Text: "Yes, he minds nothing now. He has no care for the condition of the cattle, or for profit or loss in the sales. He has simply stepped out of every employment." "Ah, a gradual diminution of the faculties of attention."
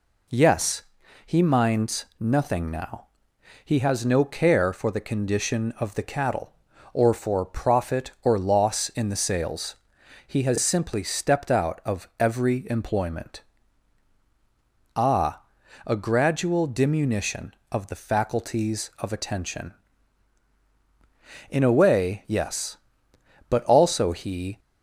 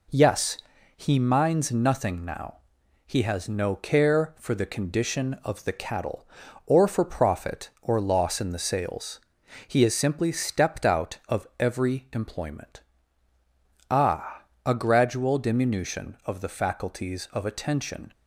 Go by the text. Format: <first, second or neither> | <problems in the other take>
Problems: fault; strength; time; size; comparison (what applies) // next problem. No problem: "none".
second | goes on to say "In a way yes But also he"; strong; from 21.4 s on; 3.1 s long